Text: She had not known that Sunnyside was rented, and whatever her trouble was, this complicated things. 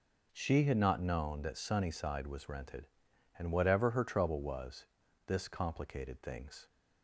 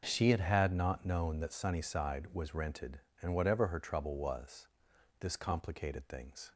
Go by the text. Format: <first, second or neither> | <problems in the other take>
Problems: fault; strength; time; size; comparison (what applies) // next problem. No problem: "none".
first | says "had" twice; at 0.4 s